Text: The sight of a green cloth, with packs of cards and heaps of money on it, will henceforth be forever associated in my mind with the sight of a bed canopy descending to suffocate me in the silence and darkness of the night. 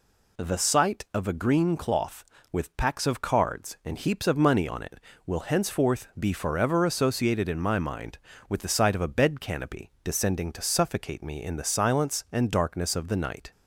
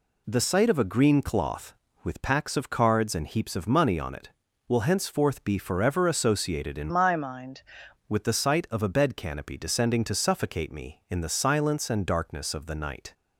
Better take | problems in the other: first | changes voice from "my" to "mind"; from 6.8 to 7.6 s; 0.8 s long

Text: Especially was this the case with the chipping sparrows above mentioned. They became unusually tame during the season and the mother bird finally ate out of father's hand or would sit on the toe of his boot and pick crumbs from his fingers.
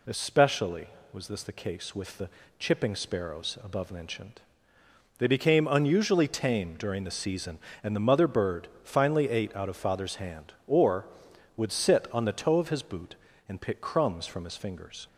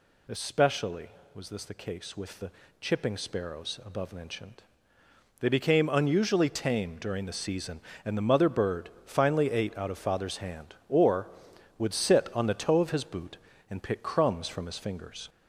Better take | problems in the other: first | gets louder; slight; throughout; 3.5 dB // pauses between "the" and "chipping"; slight; at 2.5 s; 0.30 s long; slight in the first // pauses between "bird" and "finally"; slight; at 8.8 s; 0.16 s long; slight in the first

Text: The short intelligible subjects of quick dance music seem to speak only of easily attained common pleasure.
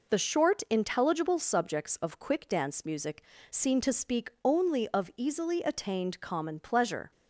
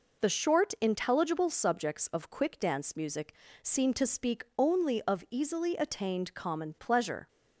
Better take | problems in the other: neither | pauses between "music" and "seem"; slight; the same in both

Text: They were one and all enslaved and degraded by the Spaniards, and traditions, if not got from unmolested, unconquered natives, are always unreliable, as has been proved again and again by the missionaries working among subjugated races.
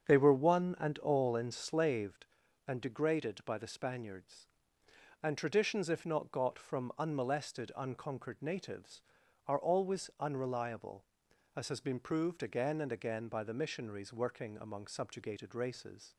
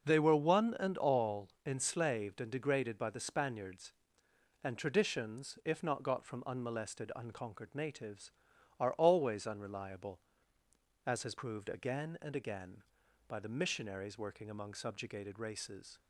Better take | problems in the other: first | starts louder than the rest; until 1.1 s; 6.5 dB; strong in the first // pauses between "all" and "enslaved"; slight; at 1.4 s; 0.18 s long // skips "been"; at 11.3 s

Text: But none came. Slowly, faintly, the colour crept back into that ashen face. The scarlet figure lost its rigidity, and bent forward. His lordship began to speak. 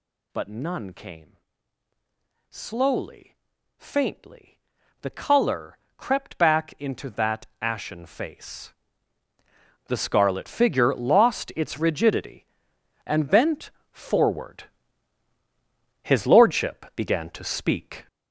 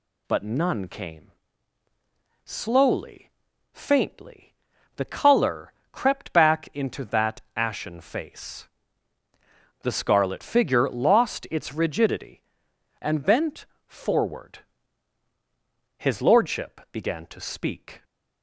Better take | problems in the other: second | gets louder; strong; throughout; 8.5 dB // pauses between "colour" and "crept"; slight; at 5.7 s; 0.18 s long; slight in the second // pauses between "bent" and "forward"; slight; at 13.7 s; 0.20 s long; slight in the second

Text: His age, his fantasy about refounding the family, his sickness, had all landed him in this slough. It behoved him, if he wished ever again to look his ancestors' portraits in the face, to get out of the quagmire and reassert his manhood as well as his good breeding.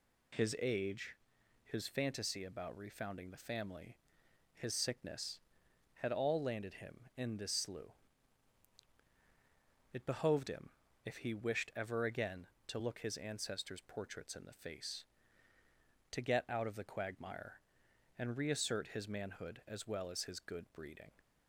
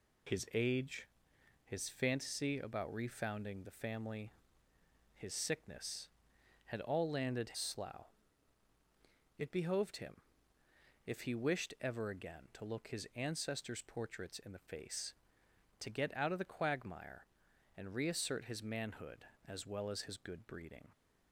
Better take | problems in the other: first | skips "him in this"; at 7.5 s

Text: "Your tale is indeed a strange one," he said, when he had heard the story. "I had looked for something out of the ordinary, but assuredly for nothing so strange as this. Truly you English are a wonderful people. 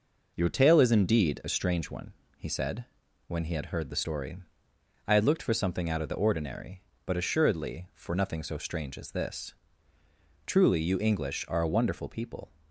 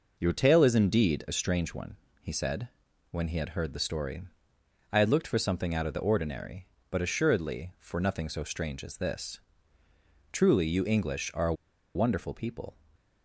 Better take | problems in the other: first | pauses between "a" and "wonderful"; at 11.5 s; 0.41 s long // stays silent after the last word; slight; from 12.7 s on; 0.5 s long

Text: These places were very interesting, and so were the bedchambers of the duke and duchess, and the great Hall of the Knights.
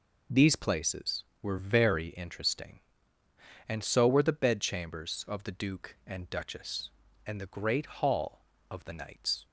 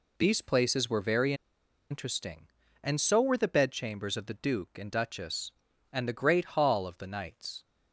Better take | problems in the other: first | pauses between "very" and "interesting"; noticeable; at 1.3 s; 0.56 s long

